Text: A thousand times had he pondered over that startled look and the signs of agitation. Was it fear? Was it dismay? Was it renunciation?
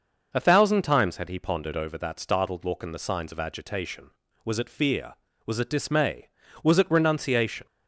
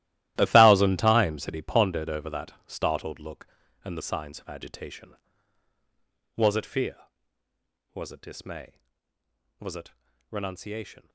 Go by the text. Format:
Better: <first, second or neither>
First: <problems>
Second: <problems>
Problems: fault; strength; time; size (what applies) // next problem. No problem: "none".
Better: first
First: none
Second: gets quieter; strong; throughout; 14.5 dB // pauses between "it" and "renunciation"; slight; at 9.9 s; 0.36 s long